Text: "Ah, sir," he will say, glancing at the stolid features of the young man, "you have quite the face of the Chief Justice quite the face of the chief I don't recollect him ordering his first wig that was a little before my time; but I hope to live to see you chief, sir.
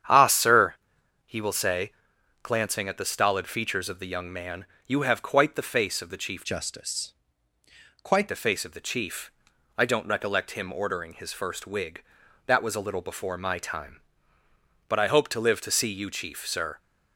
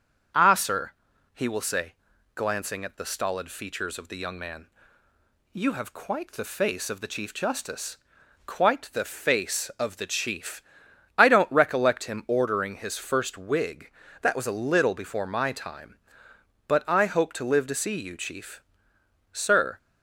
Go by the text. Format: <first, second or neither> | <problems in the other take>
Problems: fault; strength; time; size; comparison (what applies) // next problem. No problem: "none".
second | starts louder than the rest; strong; until 1.6 s; 8.5 dB // changes voice from "Justice" to "quite"; from 6.4 to 8.2 s; 1.8 s long // pauses between "Justice" and "quite"; noticeable; at 7.1 s; 0.90 s long; noticeable in the second // pauses between "chief" and "I"; noticeable; at 9.3 s; 0.46 s long; noticeable in the second